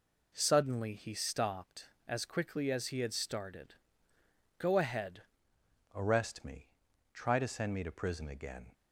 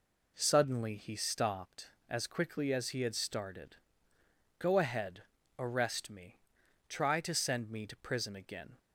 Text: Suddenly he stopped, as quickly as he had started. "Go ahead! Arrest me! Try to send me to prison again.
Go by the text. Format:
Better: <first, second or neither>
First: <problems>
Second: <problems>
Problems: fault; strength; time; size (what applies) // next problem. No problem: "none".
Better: second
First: changes voice at "Arrest"; from 5.9 s on; 2.8 s long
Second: none